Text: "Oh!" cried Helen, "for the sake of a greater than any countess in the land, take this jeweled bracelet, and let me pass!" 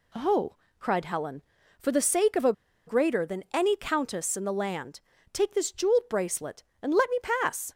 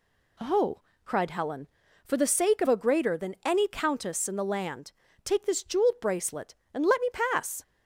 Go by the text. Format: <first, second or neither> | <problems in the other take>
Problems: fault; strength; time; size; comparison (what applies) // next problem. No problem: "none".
second | pauses between "a" and "greater"; slight; at 2.5 s; 0.34 s long